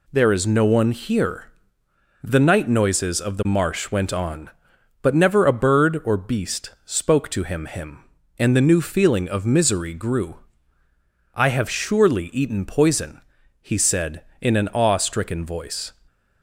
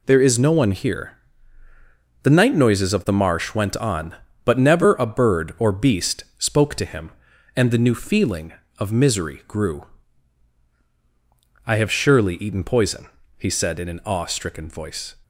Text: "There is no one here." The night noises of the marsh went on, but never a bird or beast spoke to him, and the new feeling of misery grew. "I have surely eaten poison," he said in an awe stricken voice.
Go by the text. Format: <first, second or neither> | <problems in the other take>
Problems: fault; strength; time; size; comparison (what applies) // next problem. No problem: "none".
second | pauses between "beast" and "spoke"; slight; at 6.7 s; 0.16 s long // says "him" twice; at 7.6 s